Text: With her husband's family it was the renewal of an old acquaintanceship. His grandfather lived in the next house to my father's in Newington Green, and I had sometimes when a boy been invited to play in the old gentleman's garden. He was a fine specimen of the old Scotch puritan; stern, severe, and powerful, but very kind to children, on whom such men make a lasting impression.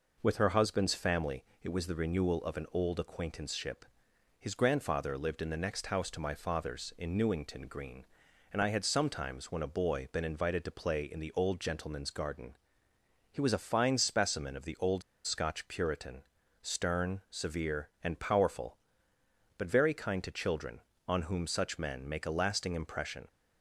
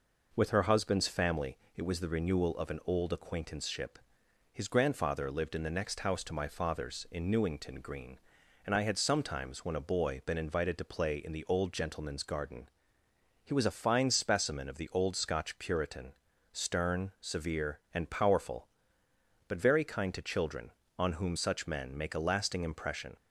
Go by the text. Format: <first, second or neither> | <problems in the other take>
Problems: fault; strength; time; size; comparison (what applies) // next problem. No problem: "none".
second | pauses between "family" and "it"; slight; at 1.4 s; 0.18 s long; slight in the second // pauses between "old" and "Scotch"; slight; at 15.0 s; 0.24 s long